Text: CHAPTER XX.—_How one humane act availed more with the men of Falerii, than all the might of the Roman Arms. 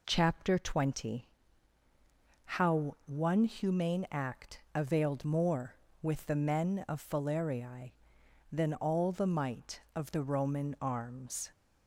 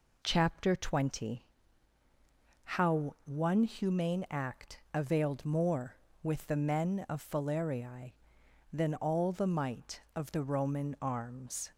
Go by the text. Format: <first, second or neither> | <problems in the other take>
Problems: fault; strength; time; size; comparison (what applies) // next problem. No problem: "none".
neither | none